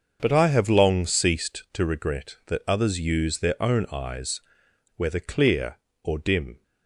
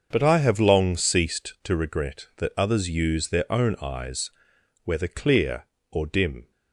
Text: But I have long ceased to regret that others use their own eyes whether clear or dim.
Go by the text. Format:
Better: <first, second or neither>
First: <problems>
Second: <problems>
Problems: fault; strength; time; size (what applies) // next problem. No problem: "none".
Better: neither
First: starts louder than the rest; until 1.2 s; 6.5 dB // pauses between "eyes" and "whether"; noticeable; at 4.4 s; 0.53 s long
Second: starts louder than the rest; until 1.1 s; 6.5 dB // pauses between "eyes" and "whether"; noticeable; at 4.3 s; 0.52 s long